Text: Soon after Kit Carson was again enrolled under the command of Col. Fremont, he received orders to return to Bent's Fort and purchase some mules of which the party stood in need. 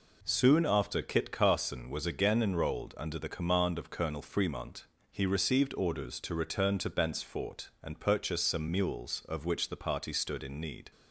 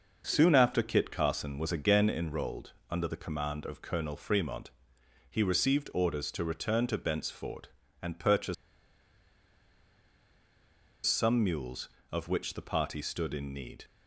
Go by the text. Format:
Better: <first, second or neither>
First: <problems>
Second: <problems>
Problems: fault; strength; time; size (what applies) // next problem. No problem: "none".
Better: first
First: none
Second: starts louder than the rest; noticeable; until 1.2 s; 6 dB // pauses between "enrolled" and "under"; slight; at 2.7 s; 0.18 s long // pauses between "purchase" and "some"; strong; at 8.5 s; 2.5 s long